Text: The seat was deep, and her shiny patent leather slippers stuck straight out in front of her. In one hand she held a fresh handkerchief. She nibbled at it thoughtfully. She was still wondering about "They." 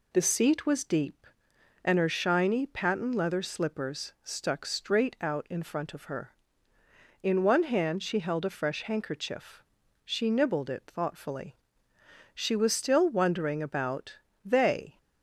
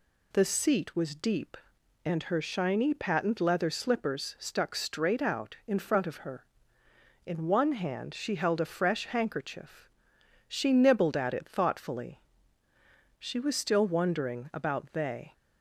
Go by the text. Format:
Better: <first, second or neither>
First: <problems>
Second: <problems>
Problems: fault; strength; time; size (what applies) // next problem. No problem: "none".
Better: second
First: skips "at"; at 10.6 s // pauses between "about" and "They"; slight; at 14.1 s; 0.26 s long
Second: none